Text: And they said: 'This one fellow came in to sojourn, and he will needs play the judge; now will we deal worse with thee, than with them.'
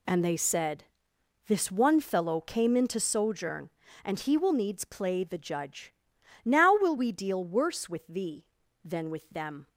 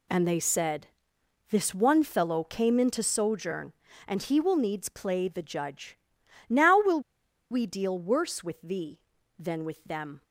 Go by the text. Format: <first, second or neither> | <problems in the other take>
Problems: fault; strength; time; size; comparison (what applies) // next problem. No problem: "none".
first | pauses between "will" and "we"; noticeable; at 7.0 s; 0.50 s long